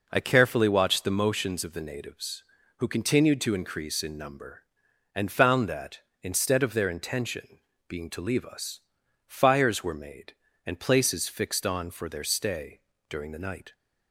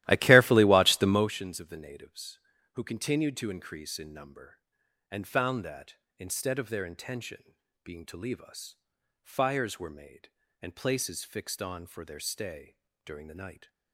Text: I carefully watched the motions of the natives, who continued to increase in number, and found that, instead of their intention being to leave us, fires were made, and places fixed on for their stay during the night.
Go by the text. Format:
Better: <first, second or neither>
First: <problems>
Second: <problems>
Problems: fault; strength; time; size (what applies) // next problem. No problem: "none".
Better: first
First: pauses between "intention" and "being"; slight; at 7.5 s; 0.30 s long // pauses between "stay" and "during"; slight; at 12.7 s; 0.30 s long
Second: starts louder than the rest; strong; until 1.3 s; 15 dB // pauses between "intention" and "being"; slight; at 7.5 s; 0.30 s long // pauses between "stay" and "during"; slight; at 12.7 s; 0.30 s long